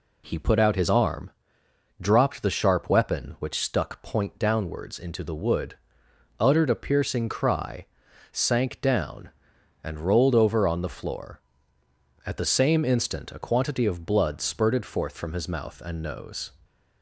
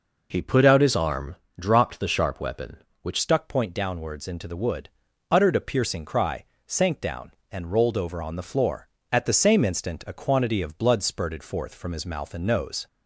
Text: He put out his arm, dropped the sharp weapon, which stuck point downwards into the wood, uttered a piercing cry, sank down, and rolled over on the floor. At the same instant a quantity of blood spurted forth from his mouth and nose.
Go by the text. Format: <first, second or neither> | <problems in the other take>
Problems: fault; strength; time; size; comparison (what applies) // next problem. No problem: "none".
first | changes voice at "stuck"; from 3.1 s on; 9.7 s long